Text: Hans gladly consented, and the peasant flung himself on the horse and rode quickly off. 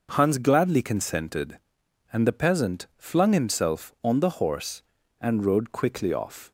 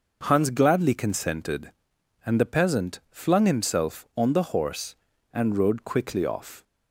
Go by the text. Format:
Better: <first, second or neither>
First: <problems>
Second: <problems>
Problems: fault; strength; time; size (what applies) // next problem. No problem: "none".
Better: neither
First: none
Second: none